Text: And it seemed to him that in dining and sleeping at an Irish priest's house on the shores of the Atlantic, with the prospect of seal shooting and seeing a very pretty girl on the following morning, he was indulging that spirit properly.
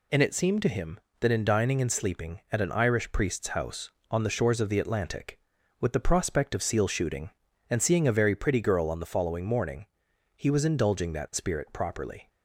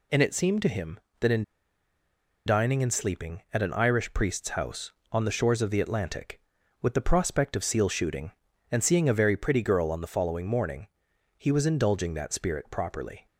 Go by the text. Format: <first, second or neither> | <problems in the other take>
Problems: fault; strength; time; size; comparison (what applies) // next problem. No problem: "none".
first | pauses between "in" and "dining"; at 1.4 s; 1.0 s long